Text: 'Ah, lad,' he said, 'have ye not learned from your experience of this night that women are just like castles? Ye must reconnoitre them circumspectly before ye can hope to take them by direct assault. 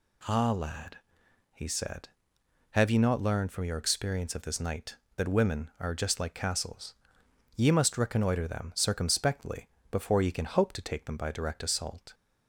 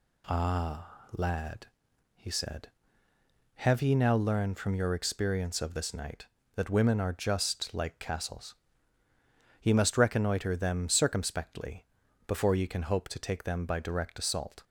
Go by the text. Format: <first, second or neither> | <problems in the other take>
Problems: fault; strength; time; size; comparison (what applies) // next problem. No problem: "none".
first | says "now" for "not"; at 3.9 s // pauses between "circumspectly" and "before"; at 11.8 s; 0.40 s long; slight in the first